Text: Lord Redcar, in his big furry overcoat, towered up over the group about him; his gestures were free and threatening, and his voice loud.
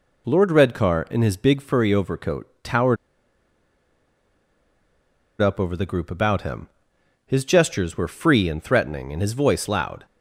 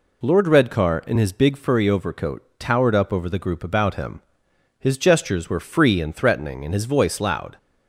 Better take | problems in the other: second | pauses between "towered" and "up"; strong; at 2.9 s; 2.4 s long

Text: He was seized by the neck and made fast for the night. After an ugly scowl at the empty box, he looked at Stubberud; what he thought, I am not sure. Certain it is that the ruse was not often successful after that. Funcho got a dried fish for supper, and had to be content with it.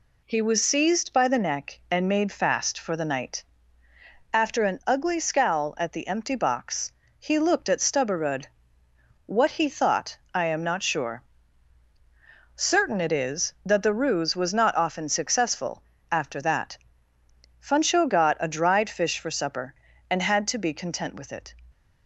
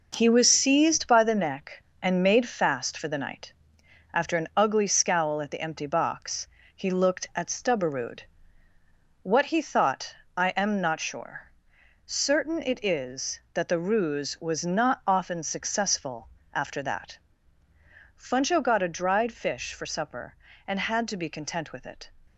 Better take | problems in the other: first | gets quieter; strong; throughout; 7.5 dB // pauses between "successful" and "after"; slight; at 16.2 s; 0.24 s long; slight in the first

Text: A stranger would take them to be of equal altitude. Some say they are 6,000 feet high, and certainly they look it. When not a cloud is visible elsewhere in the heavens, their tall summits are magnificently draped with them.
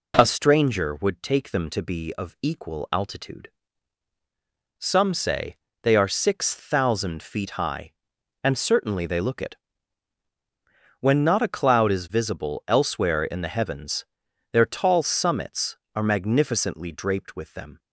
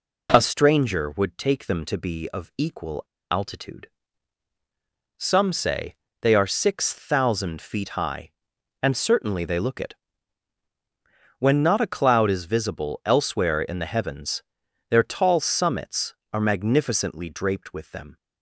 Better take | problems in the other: first | pauses between "equal" and "altitude"; slight; at 3.0 s; 0.27 s long // pauses between "say" and "they"; slight; at 5.9 s; 0.26 s long; slight in the first

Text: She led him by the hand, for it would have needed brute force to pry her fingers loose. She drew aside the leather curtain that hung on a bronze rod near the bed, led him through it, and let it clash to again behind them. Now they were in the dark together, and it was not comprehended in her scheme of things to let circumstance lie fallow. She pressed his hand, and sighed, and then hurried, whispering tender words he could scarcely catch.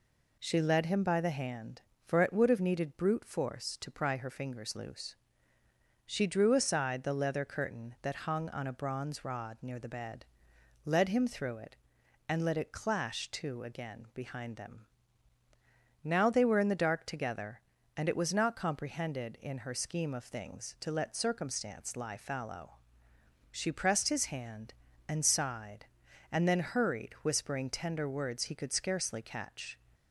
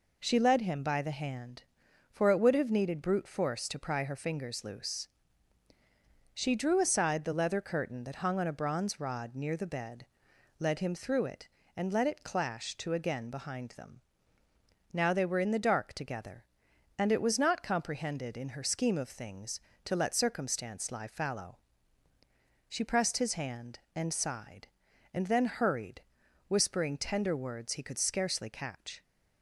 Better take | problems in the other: neither | none

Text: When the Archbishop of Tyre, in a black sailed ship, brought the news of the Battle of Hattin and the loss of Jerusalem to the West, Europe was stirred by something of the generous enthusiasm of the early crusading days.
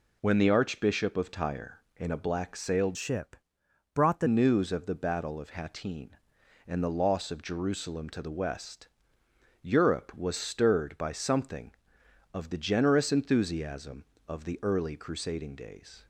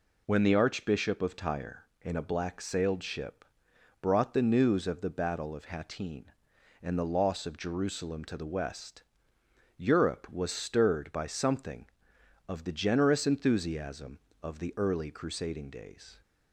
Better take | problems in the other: second | changes voice from "ship" to "the"; from 2.9 to 4.2 s; 1.3 s long

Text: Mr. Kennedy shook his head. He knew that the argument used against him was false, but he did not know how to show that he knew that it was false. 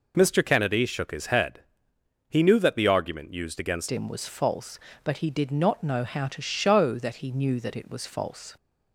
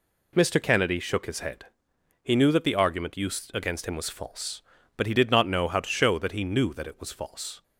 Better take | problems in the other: second | changes voice at "him"; from 3.9 s on; 4.6 s long

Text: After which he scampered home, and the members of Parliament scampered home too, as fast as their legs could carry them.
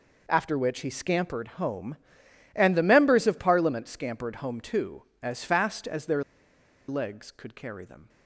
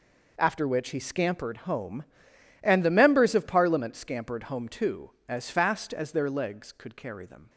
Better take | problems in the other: second | pauses between "their" and "legs"; noticeable; at 6.2 s; 0.65 s long

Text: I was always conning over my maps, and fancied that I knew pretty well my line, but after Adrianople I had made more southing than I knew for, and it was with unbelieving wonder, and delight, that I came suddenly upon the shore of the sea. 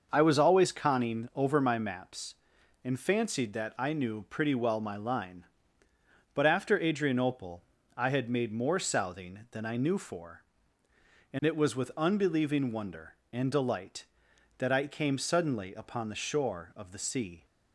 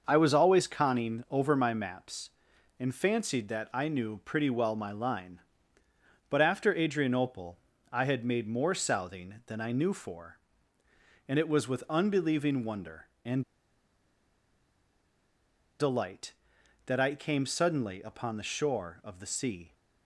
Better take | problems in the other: first | starts louder than the rest; noticeable; until 1.0 s; 6 dB; noticeable in the first // pauses between "Adrianople" and "I"; slight; at 7.5 s; 0.32 s long; slight in the first // pauses between "and" and "delight"; strong; at 13.4 s; 2.3 s long

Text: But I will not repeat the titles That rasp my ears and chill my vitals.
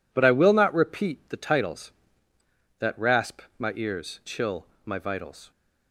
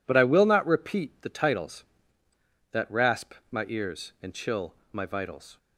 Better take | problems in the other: second | pauses between "rasp" and "my"; slight; at 3.3 s; 0.18 s long; slight in the second // skips "and"; at 4.2 s // pauses between "chill" and "my"; slight; at 4.6 s; 0.18 s long; slight in the second

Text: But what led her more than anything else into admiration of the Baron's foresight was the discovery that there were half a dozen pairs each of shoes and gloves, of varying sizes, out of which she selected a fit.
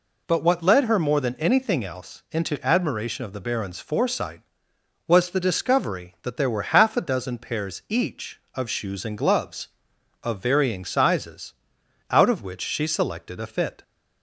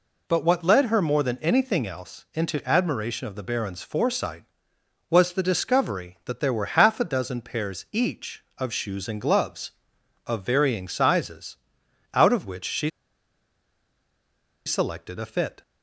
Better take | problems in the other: first | pauses between "she" and "selected"; strong; at 12.8 s; 1.7 s long

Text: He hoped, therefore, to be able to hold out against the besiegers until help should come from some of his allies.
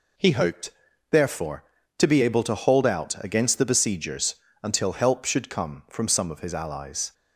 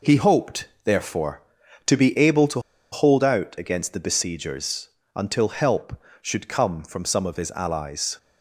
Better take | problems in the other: first | pauses between "to" and "hold"; slight; at 2.5 s; 0.32 s long // pauses between "besiegers" and "until"; slight; at 4.8 s; 0.26 s long; slight in the first

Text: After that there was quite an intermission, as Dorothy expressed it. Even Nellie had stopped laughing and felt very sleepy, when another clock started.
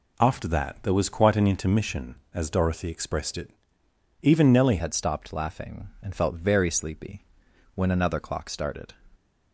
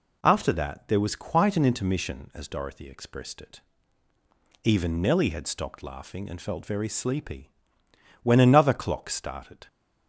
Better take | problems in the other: second | changes voice at "had"; from 4.7 s on; 4.2 s long

